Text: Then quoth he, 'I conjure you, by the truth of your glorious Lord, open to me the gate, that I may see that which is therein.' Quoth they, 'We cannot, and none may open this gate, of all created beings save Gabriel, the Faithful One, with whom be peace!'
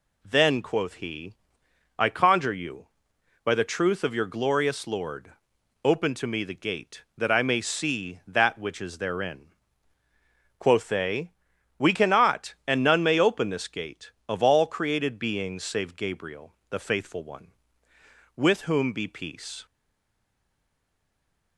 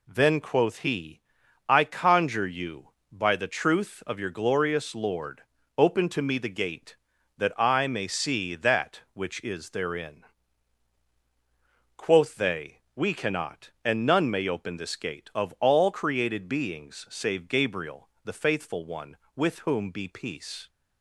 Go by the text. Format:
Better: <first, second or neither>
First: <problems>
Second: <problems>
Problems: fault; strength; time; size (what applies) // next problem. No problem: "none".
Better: second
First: stays silent after the last word; noticeable; from 19.6 s on; 1.9 s long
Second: none